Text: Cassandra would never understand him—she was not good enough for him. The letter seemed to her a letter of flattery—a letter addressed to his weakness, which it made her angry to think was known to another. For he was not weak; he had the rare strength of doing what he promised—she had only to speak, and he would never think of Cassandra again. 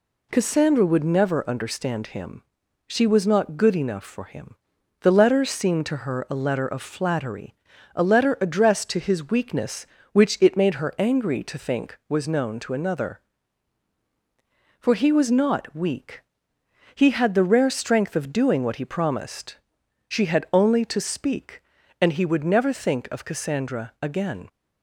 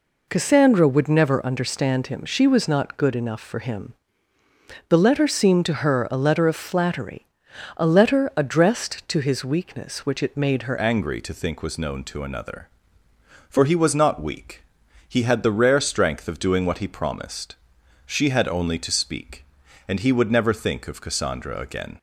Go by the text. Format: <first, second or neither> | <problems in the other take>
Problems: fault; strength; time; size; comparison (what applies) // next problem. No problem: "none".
first | changes voice at "angry"; from 10.7 s on; 11.2 s long